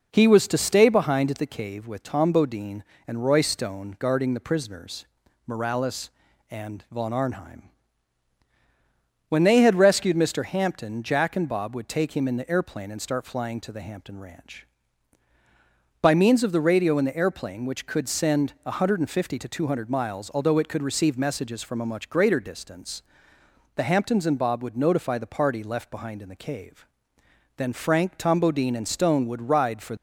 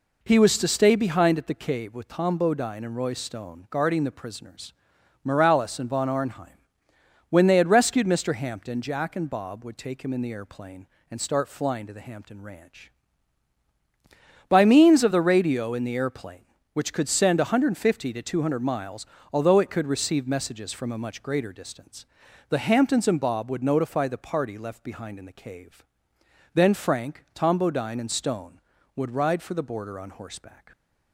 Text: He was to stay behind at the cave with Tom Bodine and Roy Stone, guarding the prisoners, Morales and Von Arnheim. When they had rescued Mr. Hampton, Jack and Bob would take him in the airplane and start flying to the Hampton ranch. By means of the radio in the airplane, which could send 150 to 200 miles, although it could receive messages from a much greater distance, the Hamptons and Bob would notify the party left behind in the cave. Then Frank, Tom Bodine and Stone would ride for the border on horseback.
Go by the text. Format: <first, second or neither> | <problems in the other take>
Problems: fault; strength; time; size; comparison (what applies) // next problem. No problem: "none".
second | stops before "the border on horseback"; at 29.9 s